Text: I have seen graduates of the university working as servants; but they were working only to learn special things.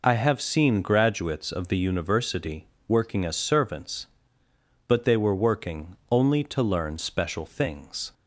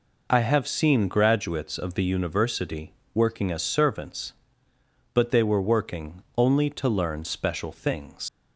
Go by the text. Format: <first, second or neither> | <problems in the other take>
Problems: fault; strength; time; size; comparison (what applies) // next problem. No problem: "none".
first | pauses between "university" and "working"; slight; at 2.9 s; 0.20 s long; slight in the first // leaves "things" unfinished; at 8.2 s; 110 ms